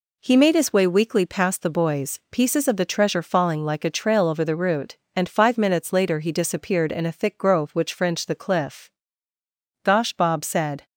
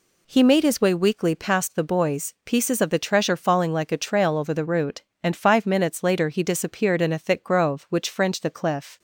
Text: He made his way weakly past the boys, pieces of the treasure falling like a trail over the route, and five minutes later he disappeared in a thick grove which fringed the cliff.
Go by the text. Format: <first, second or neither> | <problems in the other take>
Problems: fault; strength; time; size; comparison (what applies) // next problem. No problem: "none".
second | goes on to say "Gosh Bob said"; noticeable; from 9.8 s on; 1.0 s long